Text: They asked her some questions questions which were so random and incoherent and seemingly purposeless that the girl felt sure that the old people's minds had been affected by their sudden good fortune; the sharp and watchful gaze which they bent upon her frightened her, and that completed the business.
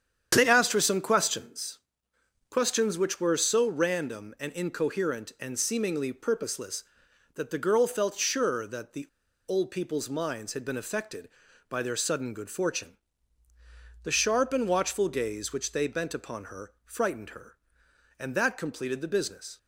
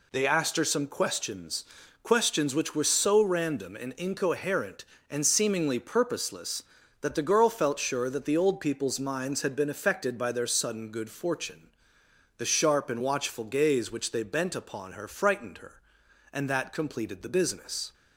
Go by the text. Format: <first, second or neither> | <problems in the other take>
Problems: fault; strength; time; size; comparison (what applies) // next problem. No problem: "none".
second | starts louder than the rest; strong; until 1.3 s; 8.5 dB // pauses between "questions" and "questions"; noticeable; at 1.7 s; 0.72 s long; also in the second // pauses between "the" and "old"; at 9.0 s; 0.40 s long